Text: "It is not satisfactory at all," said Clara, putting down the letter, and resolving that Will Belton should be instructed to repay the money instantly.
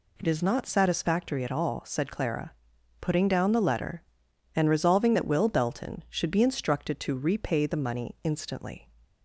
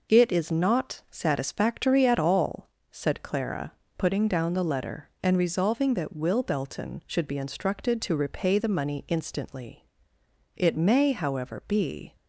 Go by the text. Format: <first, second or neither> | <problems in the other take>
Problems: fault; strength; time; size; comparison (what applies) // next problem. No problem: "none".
first | goes on to say "It may however be"; from 10.5 s on; 1.6 s long